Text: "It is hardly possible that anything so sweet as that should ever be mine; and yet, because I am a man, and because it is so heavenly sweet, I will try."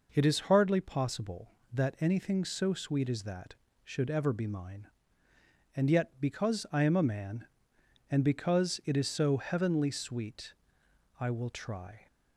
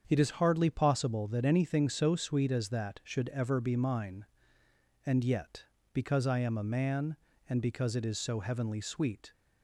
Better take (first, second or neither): first